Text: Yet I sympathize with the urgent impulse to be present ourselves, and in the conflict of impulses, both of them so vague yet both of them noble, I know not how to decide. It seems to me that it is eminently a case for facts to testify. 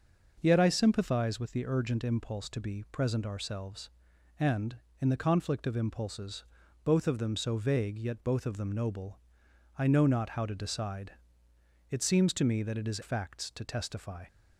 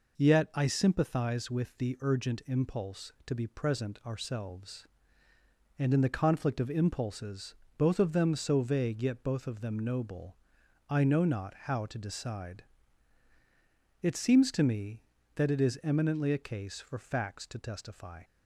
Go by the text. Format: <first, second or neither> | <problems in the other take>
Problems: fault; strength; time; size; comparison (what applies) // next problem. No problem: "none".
second | skips "eminently a case for"; at 13.0 s